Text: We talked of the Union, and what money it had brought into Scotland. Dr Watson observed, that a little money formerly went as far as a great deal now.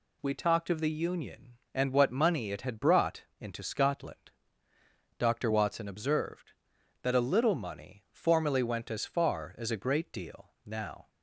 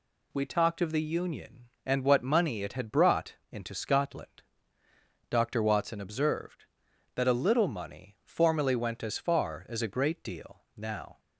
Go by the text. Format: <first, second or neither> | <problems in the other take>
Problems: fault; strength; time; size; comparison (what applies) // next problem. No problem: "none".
neither | pauses between "brought" and "into"; slight; the same in both // pauses between "deal" and "now"; slight; the same in both